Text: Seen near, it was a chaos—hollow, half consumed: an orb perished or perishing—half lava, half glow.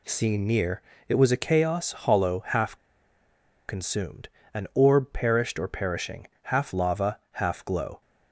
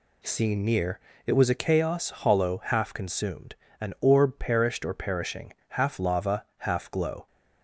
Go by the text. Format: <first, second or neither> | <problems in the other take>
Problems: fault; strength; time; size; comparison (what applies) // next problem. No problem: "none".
second | pauses between "half" and "consumed"; noticeable; at 2.7 s; 0.92 s long